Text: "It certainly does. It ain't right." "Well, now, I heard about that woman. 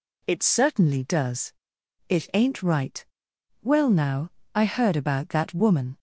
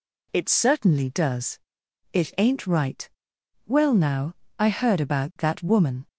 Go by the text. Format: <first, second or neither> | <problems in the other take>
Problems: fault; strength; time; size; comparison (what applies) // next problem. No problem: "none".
neither | none